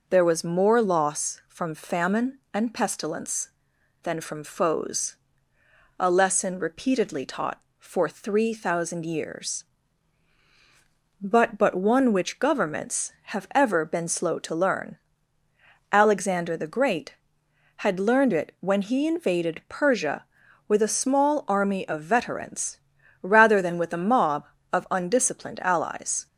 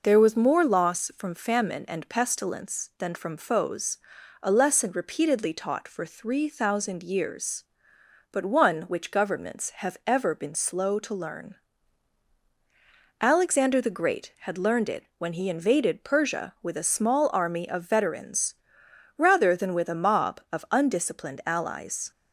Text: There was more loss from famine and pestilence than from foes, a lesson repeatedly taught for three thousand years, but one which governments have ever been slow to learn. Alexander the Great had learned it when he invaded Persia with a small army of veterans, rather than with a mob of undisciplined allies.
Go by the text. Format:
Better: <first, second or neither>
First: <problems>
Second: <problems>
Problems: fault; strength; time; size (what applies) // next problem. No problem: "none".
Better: second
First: says "but" twice; at 11.5 s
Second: none